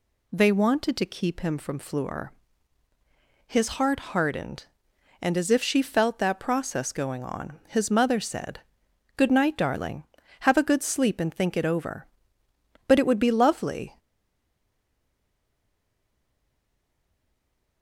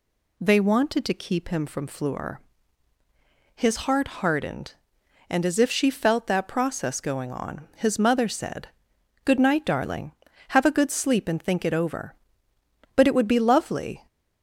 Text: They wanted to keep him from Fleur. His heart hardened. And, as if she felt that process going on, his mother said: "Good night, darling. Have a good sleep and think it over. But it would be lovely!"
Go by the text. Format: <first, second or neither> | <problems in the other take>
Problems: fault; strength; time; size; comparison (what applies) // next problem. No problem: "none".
second | stays silent after the last word; strong; from 13.9 s on; 3.9 s long